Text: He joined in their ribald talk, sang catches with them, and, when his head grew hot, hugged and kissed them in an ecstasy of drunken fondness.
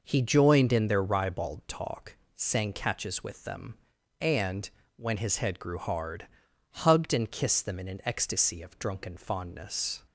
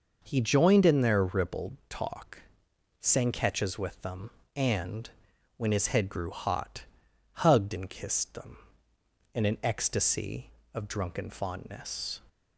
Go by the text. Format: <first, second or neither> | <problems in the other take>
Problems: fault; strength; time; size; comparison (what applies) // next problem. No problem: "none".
second | says "hard" for "hot"; at 5.7 s